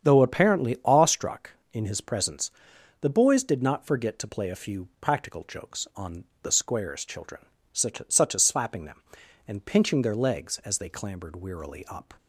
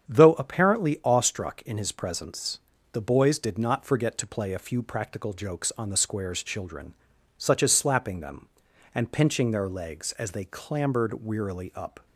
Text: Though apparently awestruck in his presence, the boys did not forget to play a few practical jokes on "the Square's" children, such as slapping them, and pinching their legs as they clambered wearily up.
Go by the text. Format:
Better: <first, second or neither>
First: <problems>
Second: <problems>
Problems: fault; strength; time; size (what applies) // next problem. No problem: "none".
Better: second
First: starts louder than the rest; strong; until 1.0 s; 8 dB // pauses between "on" and "the"; slight; at 6.2 s; 0.20 s long // says "such" twice; at 8.0 s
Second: starts louder than the rest; strong; until 1.1 s; 8 dB